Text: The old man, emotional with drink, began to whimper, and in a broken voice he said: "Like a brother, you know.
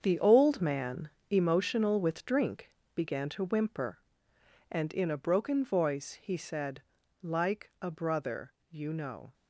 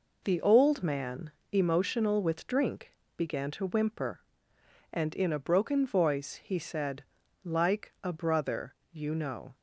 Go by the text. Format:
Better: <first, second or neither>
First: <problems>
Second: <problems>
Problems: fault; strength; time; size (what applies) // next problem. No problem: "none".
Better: second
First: gets quieter; strong; throughout; 10.5 dB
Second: none